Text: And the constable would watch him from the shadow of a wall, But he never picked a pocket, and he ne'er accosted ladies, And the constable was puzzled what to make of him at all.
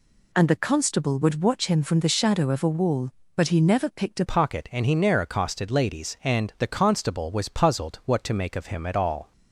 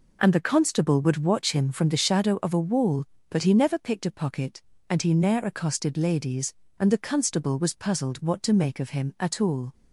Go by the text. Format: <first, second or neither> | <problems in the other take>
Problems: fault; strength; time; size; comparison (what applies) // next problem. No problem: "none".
second | changes voice at "pocket"; from 4.2 s on; 5.1 s long